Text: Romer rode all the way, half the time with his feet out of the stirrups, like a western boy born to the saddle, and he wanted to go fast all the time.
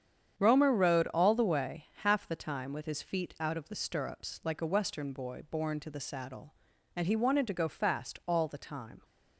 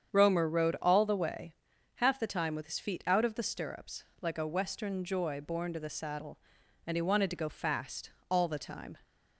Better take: first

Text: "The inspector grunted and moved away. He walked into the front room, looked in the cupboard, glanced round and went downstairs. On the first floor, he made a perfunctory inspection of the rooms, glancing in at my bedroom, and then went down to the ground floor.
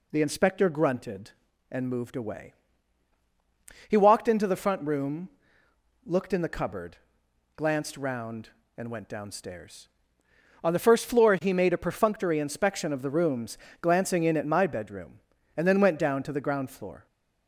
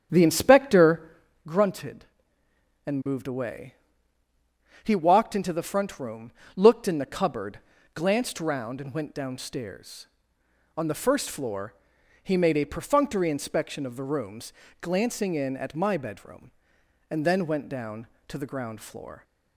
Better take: first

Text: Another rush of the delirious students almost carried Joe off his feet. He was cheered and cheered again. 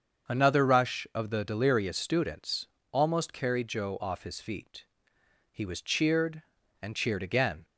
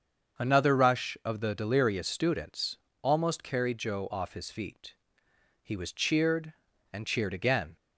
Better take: neither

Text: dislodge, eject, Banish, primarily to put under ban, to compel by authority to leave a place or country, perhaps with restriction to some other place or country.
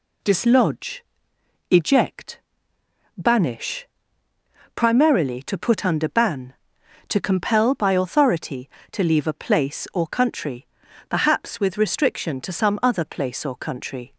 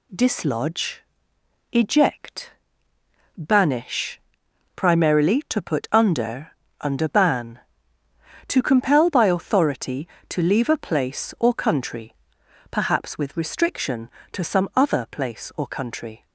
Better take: first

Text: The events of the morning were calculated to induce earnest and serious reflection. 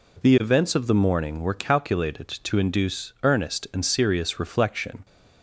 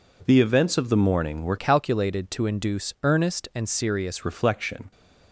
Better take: first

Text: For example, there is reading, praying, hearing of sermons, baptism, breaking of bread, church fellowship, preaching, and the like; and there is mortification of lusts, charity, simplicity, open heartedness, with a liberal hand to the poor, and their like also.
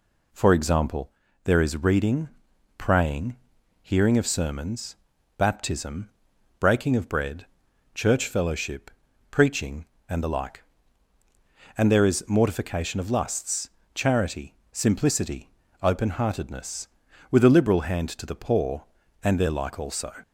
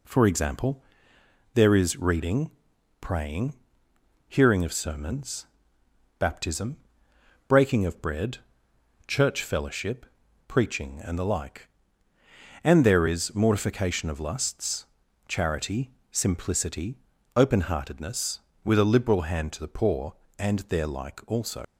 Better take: first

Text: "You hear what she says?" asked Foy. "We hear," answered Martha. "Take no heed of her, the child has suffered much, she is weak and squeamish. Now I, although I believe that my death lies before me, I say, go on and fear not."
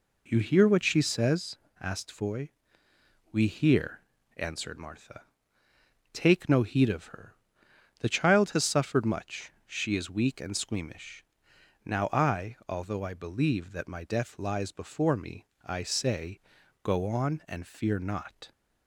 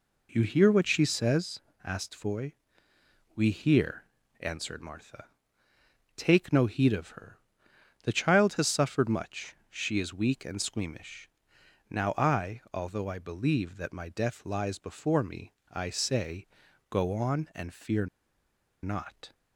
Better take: first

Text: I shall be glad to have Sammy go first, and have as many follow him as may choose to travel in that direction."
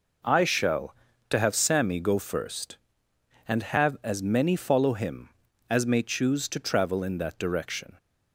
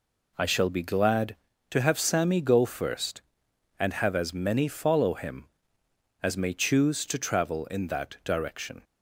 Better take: second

